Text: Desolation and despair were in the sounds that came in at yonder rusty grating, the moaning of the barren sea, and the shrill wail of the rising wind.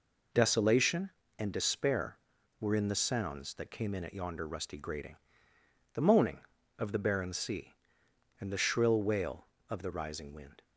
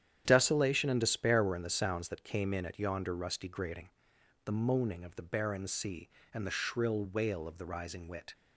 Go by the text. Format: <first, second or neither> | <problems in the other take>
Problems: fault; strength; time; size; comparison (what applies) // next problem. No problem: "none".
first | starts louder than the rest; strong; until 1.2 s; 9.5 dB // says "wit" for "wind"; at 8.0 s